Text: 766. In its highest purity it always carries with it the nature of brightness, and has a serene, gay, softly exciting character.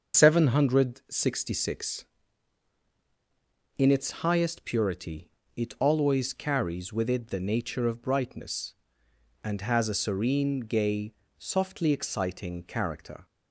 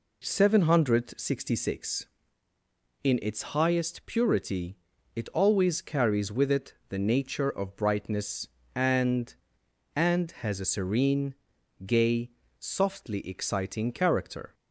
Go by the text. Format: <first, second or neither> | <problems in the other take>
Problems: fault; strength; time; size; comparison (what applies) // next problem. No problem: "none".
first | pauses between "purity" and "it"; at 4.7 s; 0.40 s long; slight in the first // pauses between "it" and "the"; slight; at 6.7 s; 0.16 s long // says "and" twice; at 9.9 s